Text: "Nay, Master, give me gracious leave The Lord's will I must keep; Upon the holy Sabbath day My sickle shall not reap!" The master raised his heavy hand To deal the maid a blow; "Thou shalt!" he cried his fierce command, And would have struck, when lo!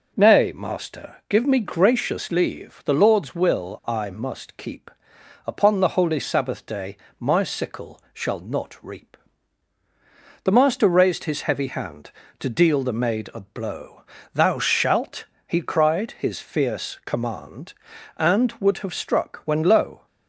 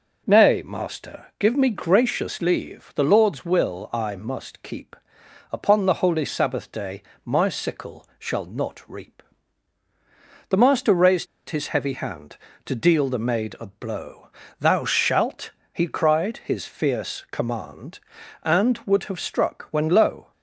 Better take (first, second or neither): first